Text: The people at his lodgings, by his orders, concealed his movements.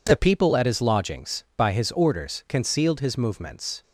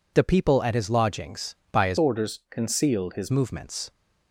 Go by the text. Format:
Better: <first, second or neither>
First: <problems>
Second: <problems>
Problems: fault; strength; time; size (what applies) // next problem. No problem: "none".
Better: first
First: none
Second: changes voice from "orders" to "his"; from 1.9 to 3.3 s; 1.4 s long